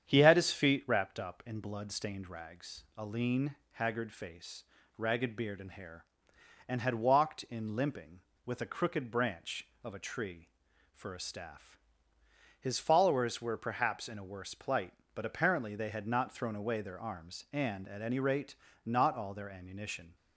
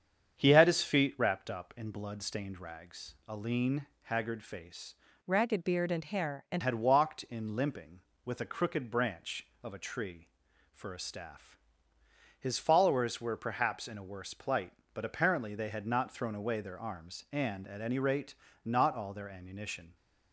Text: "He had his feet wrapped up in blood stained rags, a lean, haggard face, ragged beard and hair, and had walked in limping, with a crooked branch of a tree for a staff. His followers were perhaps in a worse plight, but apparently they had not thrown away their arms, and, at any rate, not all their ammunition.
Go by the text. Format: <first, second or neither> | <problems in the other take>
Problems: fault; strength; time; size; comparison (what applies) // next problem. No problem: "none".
first | starts louder than the rest; strong; until 1.4 s; 7.5 dB; strong in the first // changes voice from "ragged" to "and"; from 5.2 to 6.6 s; 1.4 s long